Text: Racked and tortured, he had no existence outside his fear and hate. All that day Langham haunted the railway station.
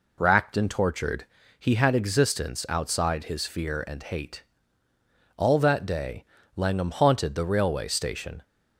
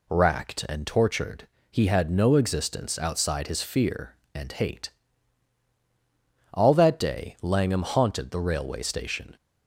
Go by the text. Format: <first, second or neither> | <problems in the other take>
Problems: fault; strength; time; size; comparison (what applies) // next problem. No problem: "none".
second | skips "no"; at 1.9 s // pauses between "day" and "Langham"; slight; at 6.2 s; 0.32 s long